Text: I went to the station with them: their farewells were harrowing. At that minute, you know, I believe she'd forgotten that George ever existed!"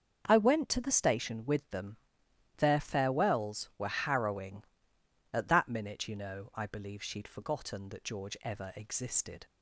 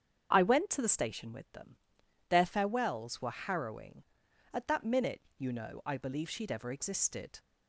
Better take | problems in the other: first | starts louder than the rest; strong; until 1.3 s; 7.5 dB; also in the first // skips "forgotten that George"; at 6.5 s

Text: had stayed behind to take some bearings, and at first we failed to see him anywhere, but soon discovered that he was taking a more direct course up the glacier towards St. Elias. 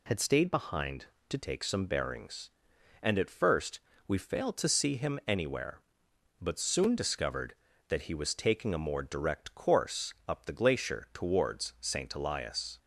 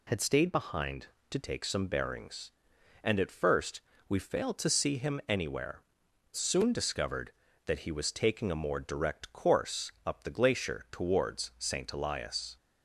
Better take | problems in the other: first | pauses between "first" and "we"; slight; at 3.7 s; 0.28 s long; slight in the first // skips "but"; at 6.0 s

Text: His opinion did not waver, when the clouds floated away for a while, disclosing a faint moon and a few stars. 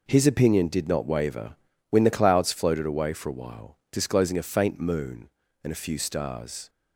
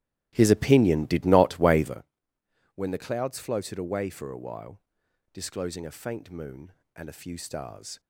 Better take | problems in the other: first | starts louder than the rest; strong; until 2.0 s; 14 dB

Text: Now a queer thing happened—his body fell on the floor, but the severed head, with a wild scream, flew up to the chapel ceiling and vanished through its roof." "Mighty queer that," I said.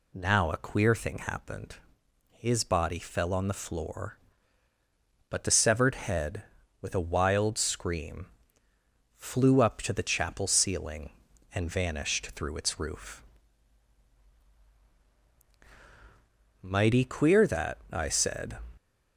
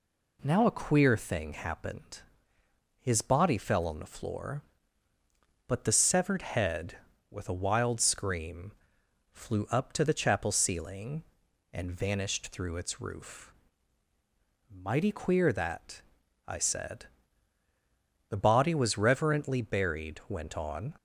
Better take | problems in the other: first | goes on to say "The body was reverently buried went on"; strong; from 18.3 s on; 2.6 s long

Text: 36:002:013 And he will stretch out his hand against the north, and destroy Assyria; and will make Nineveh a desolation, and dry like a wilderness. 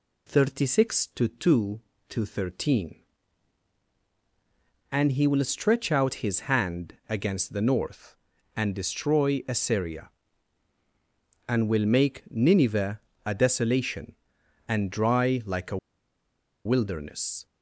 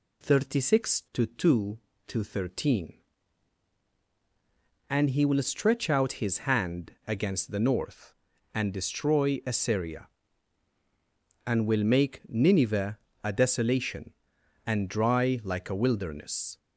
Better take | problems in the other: second | pauses between "Nineveh" and "a"; slight; at 12.9 s; 0.26 s long; slight in the second // pauses between "a" and "wilderness"; noticeable; at 15.7 s; 0.87 s long

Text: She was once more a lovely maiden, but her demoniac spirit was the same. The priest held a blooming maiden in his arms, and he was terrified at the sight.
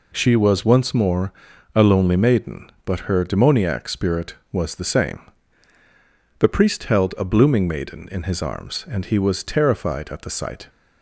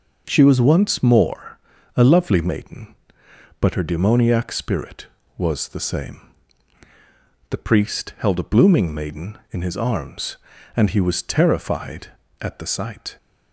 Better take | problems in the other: second | pauses between "more" and "a"; at 1.3 s; 0.42 s long; slight in the second // says "lonely" for "lovely"; at 1.8 s

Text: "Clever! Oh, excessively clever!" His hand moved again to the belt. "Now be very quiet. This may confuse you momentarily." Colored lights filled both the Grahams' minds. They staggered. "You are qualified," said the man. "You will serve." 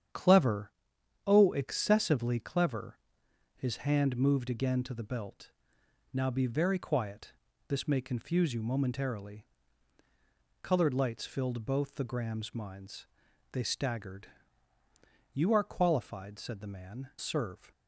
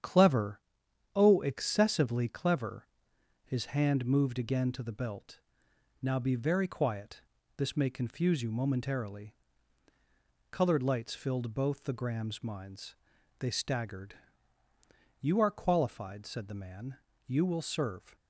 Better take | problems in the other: second | starts louder than the rest; strong; until 1.6 s; 8.5 dB; strong in the second // skips "You will"; at 17.1 s

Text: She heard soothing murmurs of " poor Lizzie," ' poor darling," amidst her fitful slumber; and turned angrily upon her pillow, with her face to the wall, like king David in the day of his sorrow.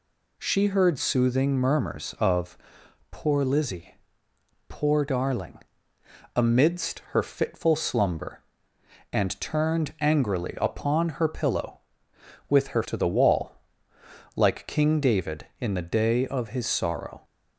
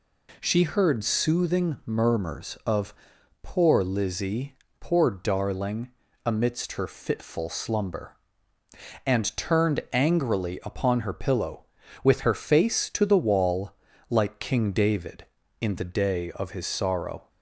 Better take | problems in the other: second | skips "face"; at 12.8 s

